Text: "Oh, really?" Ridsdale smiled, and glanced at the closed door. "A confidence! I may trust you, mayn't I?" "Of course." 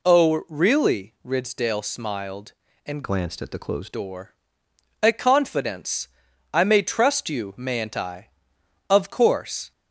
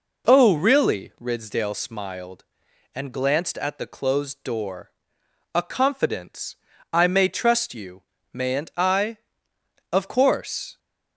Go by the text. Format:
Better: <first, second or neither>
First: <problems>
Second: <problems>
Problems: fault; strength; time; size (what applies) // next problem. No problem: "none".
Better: second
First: changes voice from "glanced" to "closed"; from 3.0 to 3.9 s; 0.9 s long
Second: none